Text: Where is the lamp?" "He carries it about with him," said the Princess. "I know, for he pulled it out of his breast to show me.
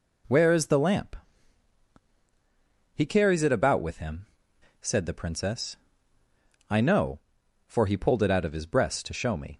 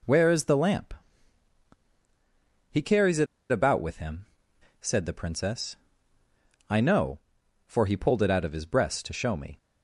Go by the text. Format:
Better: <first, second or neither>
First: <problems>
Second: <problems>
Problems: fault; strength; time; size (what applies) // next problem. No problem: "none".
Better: first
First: none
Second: pauses between "it" and "about"; slight; at 3.2 s; 0.24 s long